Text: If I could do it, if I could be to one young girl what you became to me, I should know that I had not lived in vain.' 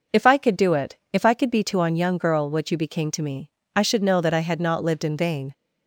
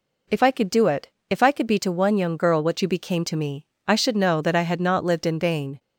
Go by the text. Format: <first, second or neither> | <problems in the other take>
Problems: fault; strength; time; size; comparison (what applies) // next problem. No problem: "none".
second | says "on" for "one"; at 1.8 s